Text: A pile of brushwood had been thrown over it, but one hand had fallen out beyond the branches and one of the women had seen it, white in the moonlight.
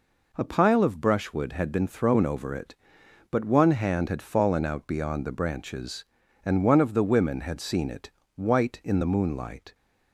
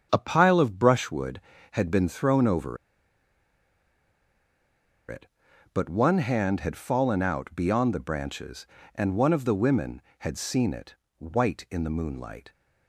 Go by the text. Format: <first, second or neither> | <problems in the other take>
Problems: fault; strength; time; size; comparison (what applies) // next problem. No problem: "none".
first | starts louder than the rest; strong; until 1.1 s; 8 dB // pauses between "over" and "it"; strong; at 2.7 s; 2.3 s long